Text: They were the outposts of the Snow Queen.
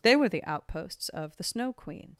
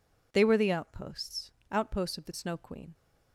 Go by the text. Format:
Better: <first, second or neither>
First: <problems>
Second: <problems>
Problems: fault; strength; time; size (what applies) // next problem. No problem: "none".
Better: first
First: none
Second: says "outposts" twice; at 1.7 s